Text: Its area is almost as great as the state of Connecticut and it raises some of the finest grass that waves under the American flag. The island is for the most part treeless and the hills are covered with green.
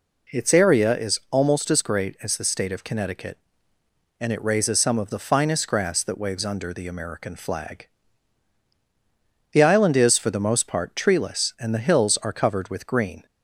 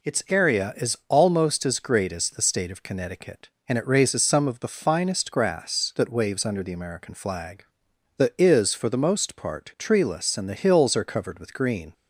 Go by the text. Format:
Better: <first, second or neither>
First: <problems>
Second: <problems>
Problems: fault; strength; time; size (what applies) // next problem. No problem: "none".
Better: first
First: none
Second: skips "island"; at 8.3 s